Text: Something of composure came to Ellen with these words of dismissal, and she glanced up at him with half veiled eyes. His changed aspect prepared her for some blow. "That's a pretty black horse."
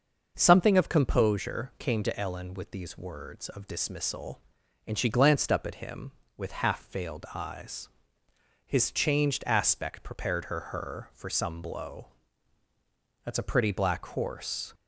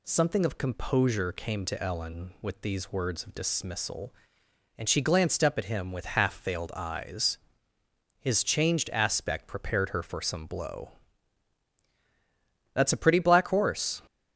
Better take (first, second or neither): second